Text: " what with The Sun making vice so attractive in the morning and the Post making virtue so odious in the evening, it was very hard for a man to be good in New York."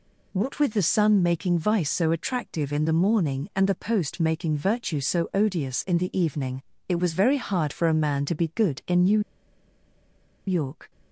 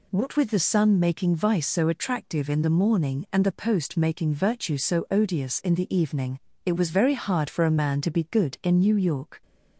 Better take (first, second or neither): second